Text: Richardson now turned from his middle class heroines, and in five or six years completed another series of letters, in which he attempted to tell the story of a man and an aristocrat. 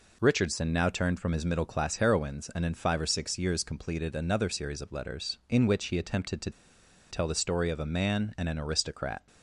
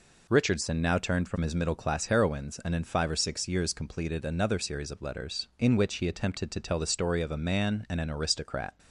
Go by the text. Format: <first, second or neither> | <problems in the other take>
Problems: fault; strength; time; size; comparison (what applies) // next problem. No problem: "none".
second | pauses between "to" and "tell"; noticeable; at 6.5 s; 0.60 s long